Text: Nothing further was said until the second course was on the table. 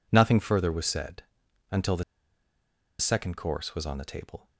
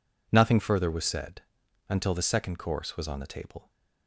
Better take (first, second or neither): second